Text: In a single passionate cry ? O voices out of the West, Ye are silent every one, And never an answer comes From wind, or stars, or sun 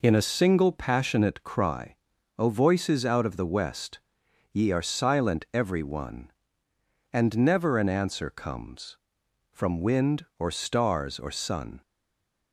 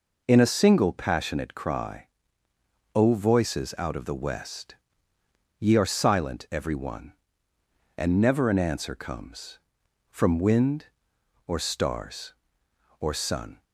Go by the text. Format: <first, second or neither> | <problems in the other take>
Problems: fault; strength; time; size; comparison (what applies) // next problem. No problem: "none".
second | stays silent after the last word; slight; from 11.8 s on; 0.7 s long